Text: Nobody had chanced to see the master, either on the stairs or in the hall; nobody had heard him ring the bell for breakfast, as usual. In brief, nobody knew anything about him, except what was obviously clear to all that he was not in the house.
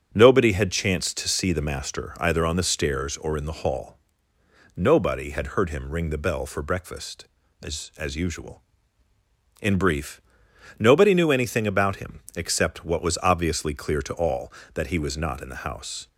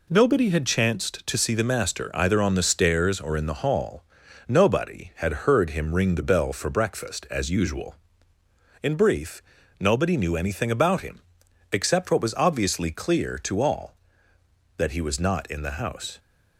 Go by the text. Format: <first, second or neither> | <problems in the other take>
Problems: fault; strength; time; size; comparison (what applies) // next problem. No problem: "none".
second | starts louder than the rest; strong; until 1.1 s; 7 dB // says "as" twice; at 7.9 s